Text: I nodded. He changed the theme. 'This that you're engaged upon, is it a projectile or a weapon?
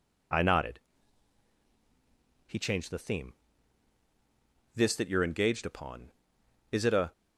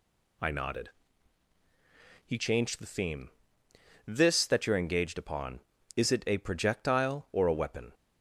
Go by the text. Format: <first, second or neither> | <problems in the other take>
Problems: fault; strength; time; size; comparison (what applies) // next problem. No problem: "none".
second | stops before "projectile or a weapon"; at 7.1 s